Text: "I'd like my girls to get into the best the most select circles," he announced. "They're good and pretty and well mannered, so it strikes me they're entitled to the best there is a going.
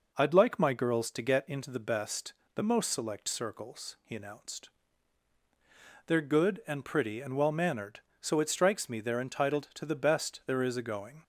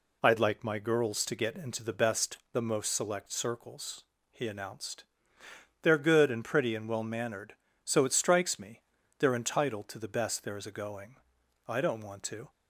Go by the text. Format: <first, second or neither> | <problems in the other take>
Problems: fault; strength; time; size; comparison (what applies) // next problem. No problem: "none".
first | pauses between "best" and "the"; slight; at 2.3 s; 0.16 s long; slight in the first // pauses between "me" and "they're"; at 8.8 s; 0.38 s long // goes on to say "I don't want to"; noticeable; from 11.6 s on; 0.86 s long